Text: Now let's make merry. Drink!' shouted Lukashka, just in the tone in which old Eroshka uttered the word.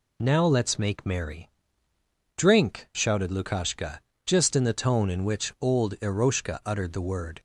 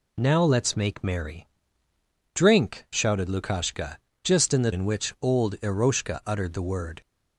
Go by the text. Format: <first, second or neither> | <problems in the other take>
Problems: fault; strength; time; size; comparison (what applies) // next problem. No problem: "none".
first | skips "tone"; at 4.7 s